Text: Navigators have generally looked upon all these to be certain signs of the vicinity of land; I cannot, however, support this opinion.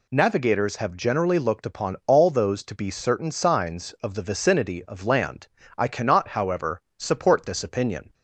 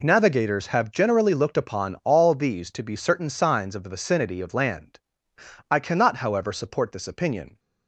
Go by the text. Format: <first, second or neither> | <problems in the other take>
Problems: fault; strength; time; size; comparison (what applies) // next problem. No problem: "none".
second | says "those" for "these"; at 2.2 s